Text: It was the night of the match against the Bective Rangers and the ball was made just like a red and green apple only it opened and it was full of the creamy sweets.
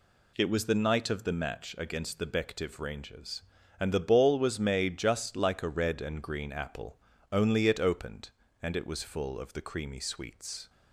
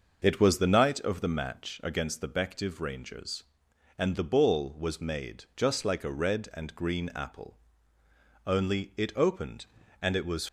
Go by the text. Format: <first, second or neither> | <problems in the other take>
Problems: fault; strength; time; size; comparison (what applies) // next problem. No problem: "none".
first | pauses between "apple" and "only"; noticeable; at 7.5 s; 0.90 s long; slight in the first // stops before "full of the creamy sweets"; at 10.4 s